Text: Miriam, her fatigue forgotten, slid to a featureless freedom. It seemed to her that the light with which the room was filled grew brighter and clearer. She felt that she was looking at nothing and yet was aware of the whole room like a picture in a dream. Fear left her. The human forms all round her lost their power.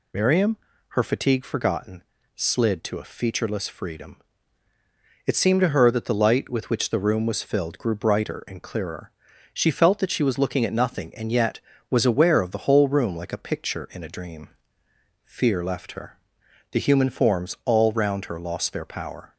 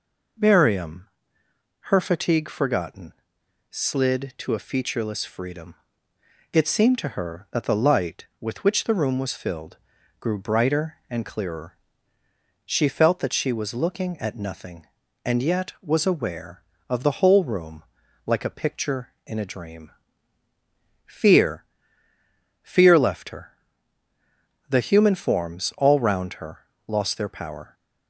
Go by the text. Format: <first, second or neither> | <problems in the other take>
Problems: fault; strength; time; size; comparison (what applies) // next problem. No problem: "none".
first | pauses between "filled" and "grew"; at 9.7 s; 0.42 s long // pauses between "room" and "like"; at 17.8 s; 0.42 s long // says "Fear" twice; at 22.6 s // pauses between "her" and "lost"; slight; at 26.5 s; 0.26 s long